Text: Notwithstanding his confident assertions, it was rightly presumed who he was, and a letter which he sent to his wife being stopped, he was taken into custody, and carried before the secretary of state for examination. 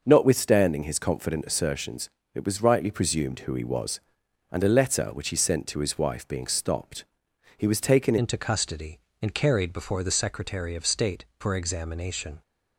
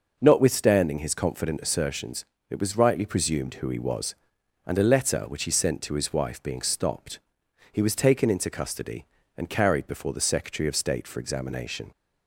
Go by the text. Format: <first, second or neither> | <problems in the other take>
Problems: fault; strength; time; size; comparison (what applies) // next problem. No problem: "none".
second | changes voice at "into"; from 8.1 s on; 4.3 s long